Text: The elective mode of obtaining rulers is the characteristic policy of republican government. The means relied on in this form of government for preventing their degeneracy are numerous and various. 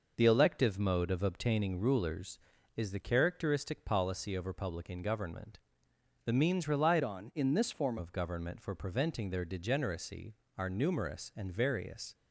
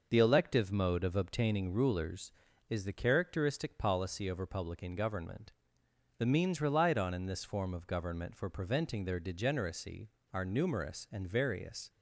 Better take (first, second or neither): second